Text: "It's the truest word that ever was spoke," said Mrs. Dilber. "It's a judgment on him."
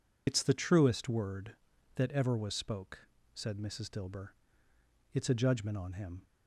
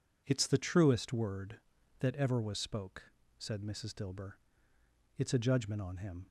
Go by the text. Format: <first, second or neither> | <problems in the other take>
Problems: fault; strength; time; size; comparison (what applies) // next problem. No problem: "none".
second | loses the start of "It's"; at 0.2 s; 55 ms